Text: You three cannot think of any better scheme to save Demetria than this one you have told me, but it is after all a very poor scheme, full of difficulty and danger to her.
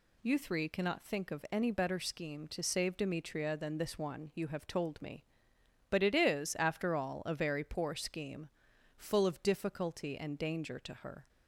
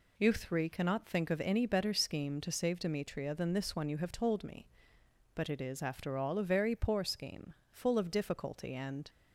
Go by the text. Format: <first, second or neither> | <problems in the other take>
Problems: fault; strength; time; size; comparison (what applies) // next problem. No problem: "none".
first | stops before "danger to her"; at 9.0 s